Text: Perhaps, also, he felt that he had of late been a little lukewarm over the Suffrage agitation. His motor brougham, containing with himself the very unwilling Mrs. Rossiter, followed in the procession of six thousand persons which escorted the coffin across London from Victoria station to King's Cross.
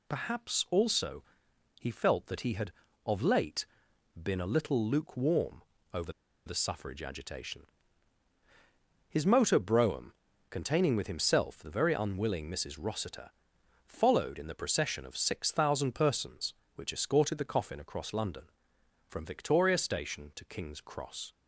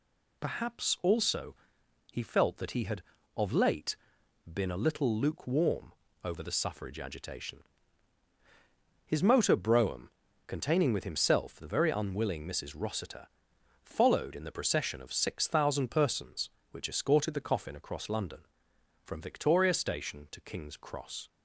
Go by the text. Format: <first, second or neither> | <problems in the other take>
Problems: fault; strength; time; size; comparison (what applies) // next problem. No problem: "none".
second | pauses between "late" and "been"; noticeable; at 3.6 s; 0.56 s long; noticeable in the second // pauses between "lukewarm" and "over"; slight; at 5.6 s; 0.30 s long; slight in the second // pauses between "over" and "the"; slight; at 6.1 s; 0.33 s long